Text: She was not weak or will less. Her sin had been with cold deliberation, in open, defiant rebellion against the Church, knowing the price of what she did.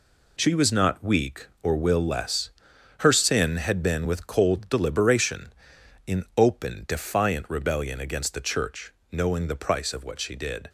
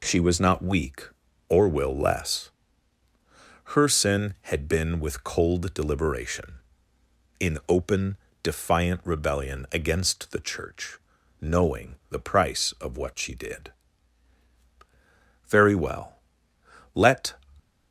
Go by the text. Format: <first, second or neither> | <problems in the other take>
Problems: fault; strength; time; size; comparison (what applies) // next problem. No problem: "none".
first | goes on to say "Very well let"; strong; from 15.4 s on; 1.8 s long